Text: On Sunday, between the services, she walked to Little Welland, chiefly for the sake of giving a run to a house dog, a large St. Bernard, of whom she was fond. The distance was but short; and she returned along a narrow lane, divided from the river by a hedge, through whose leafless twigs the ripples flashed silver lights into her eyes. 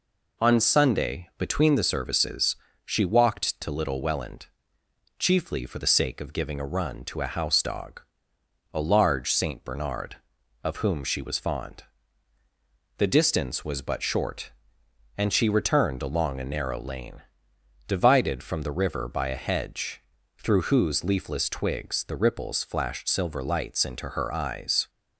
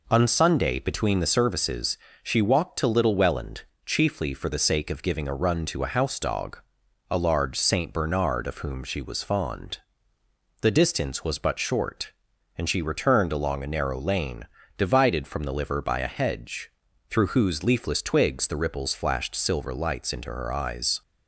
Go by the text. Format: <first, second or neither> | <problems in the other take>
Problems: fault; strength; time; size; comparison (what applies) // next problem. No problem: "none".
first | says "liver" for "river"; at 15.5 s